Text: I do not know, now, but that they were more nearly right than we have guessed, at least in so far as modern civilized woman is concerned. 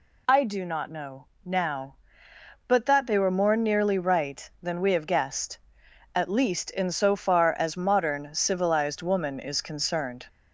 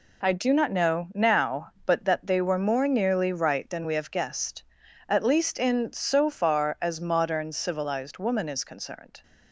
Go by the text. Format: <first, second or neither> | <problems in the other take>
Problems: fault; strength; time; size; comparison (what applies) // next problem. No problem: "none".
first | gets quieter; strong; throughout; 8 dB